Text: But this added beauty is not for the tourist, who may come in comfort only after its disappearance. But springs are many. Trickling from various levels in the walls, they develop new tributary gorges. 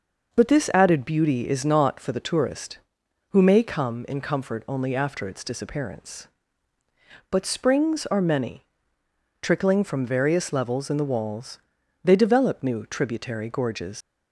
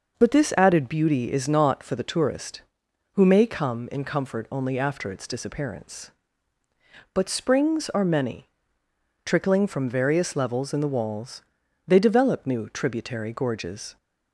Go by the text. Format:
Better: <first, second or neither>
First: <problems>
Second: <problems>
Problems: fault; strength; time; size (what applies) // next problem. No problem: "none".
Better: second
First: leaves "gorges" unfinished; at 14.0 s; 130 ms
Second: none